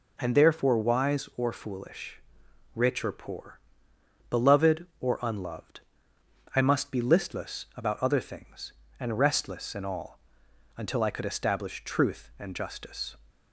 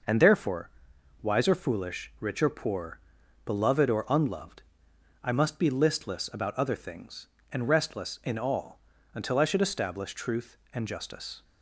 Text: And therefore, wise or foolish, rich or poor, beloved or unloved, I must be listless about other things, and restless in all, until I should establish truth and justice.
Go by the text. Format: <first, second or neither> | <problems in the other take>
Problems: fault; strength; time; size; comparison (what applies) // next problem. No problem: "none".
second | says "could" for "should"; at 11.1 s